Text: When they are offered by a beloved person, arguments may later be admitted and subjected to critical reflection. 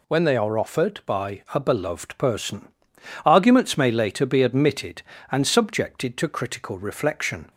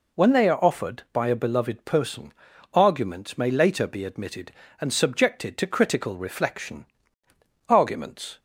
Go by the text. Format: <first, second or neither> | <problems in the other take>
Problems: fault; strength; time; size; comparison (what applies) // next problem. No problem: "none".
first | goes on to say "Arguments"; noticeable; from 7.6 s on; 0.70 s long